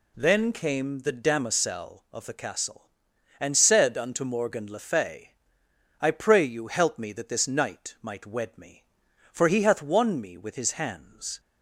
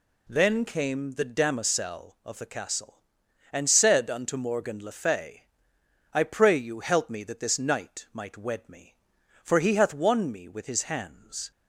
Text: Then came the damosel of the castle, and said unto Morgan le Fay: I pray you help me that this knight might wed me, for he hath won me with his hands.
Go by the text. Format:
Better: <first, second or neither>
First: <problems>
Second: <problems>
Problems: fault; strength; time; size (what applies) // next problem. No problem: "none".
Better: neither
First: none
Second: none